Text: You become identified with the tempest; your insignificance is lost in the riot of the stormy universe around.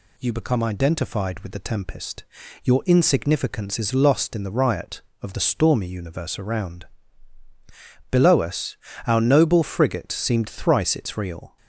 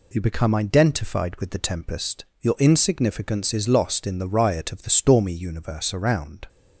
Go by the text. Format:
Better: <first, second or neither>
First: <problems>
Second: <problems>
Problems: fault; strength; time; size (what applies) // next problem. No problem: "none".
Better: second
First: goes on to say "Below us our noble frigate seemed thrice its real"; strong; from 8.1 s on; 3.4 s long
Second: none